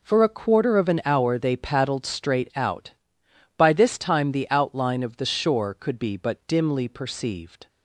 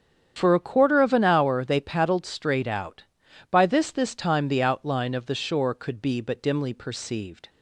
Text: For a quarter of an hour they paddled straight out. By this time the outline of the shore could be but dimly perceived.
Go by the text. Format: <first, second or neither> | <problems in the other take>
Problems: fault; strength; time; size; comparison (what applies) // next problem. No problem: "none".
first | starts louder than the rest; strong; until 1.3 s; 8.5 dB // says "this" twice; at 3.8 s